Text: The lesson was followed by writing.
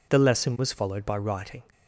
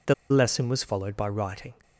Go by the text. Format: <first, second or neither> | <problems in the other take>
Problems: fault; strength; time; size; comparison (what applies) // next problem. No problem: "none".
first | pauses between "The" and "lesson"; slight; at 0.1 s; 0.16 s long